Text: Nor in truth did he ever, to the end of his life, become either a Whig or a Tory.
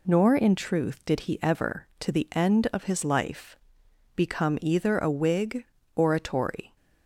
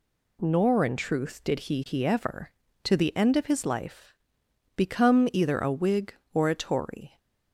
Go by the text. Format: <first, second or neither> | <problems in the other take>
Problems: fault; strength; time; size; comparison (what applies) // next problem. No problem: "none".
first | says "he" twice; at 1.8 s